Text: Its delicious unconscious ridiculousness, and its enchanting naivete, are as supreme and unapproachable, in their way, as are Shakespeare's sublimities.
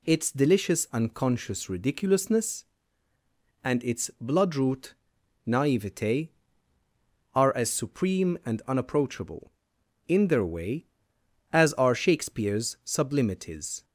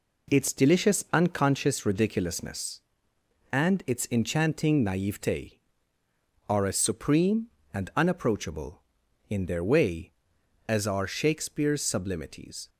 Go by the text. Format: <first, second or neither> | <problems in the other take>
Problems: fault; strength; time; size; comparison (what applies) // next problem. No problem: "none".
second | says "bloodroot" for "enchanting"; at 4.2 s